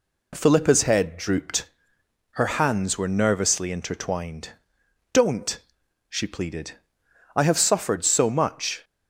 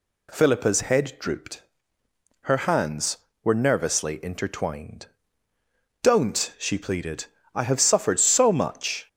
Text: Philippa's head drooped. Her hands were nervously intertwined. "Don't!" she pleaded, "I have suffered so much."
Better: neither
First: none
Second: none

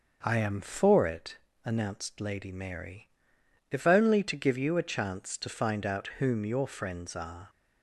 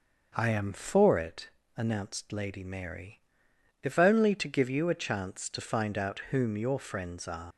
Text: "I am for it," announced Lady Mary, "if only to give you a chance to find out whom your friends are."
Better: first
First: none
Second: leaves "are" unfinished; at 7.5 s; 105 ms

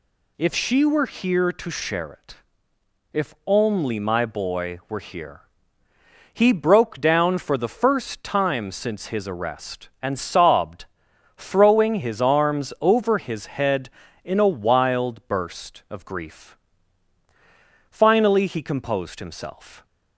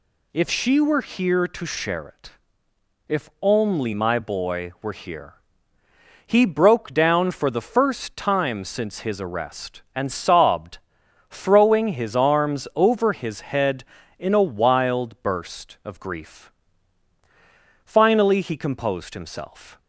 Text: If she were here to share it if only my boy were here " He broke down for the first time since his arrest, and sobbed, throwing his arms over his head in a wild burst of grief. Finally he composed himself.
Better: neither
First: pauses between "it" and "if"; noticeable; at 2.3 s; 0.76 s long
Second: pauses between "it" and "if"; noticeable; at 2.3 s; 0.76 s long

